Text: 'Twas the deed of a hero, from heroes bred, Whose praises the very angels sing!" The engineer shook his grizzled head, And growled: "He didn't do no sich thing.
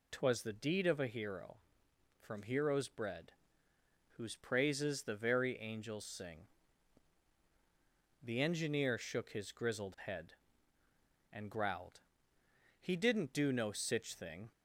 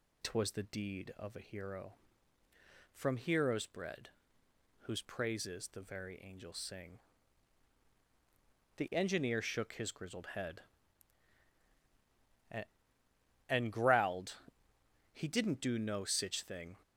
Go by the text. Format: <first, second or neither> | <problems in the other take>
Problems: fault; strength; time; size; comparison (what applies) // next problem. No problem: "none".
first | says "And" twice; at 13.4 s